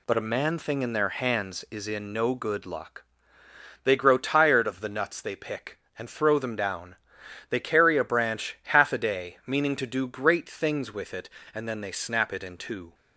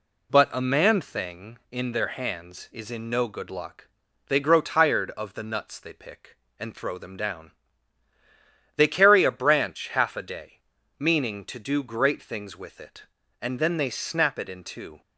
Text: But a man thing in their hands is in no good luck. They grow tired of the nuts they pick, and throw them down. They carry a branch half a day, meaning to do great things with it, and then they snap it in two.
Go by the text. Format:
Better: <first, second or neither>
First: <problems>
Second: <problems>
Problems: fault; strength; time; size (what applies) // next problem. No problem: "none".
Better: neither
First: none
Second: none